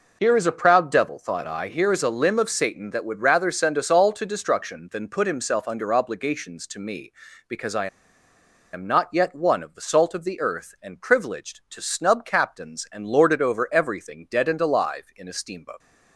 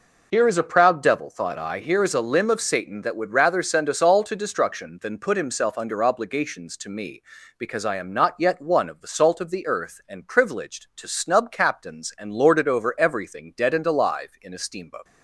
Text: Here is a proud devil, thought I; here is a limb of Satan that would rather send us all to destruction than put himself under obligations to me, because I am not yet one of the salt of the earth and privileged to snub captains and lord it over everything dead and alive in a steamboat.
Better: second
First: pauses between "I" and "am"; noticeable; at 7.8 s; 0.86 s long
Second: none

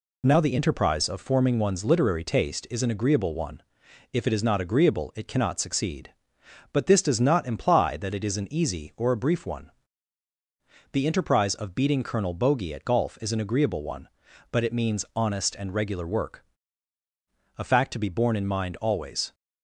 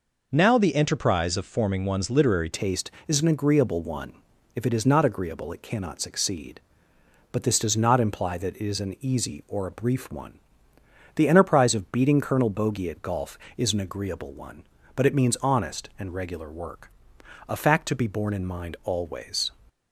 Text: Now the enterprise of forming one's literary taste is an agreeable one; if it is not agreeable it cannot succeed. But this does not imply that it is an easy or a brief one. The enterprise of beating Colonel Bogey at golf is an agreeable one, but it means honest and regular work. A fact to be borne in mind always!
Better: first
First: none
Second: changes voice at "taste"; from 2.5 s on; 17.0 s long

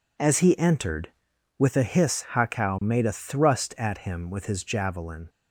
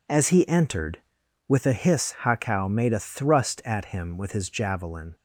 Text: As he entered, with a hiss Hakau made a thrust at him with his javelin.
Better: neither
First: none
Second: none

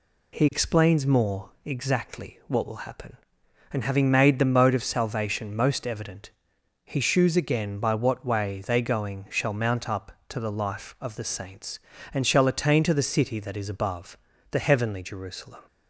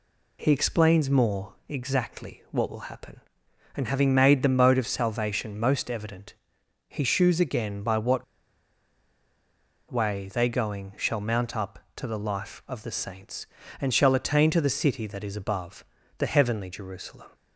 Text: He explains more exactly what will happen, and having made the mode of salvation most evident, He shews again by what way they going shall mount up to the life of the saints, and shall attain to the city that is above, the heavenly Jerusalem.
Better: first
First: pauses between "more" and "exactly"; slight; at 1.4 s; 0.16 s long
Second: pauses between "more" and "exactly"; slight; at 1.5 s; 0.16 s long // pauses between "what" and "way"; strong; at 8.2 s; 1.6 s long

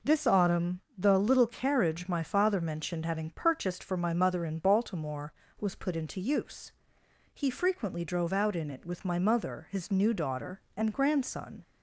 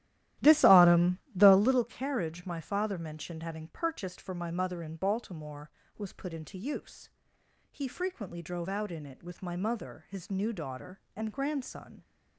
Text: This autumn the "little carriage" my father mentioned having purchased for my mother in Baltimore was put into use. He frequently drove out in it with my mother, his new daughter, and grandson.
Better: first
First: pauses between "autumn" and "the"; slight; at 0.8 s; 0.16 s long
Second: starts louder than the rest; strong; until 1.8 s; 14 dB // pauses between "autumn" and "the"; slight; at 1.1 s; 0.16 s long

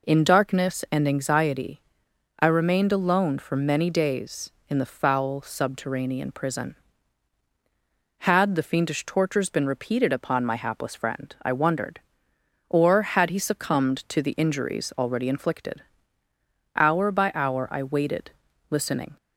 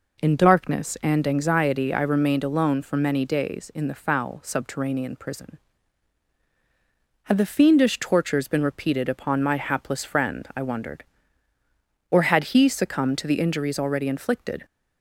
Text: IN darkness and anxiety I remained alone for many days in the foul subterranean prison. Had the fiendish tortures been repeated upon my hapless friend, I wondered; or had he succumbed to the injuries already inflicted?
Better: second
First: pauses between "anxiety" and "I"; noticeable; at 1.8 s; 0.58 s long // goes on to say "Hour by hour I waited listening"; strong; from 16.7 s on; 2.4 s long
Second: none

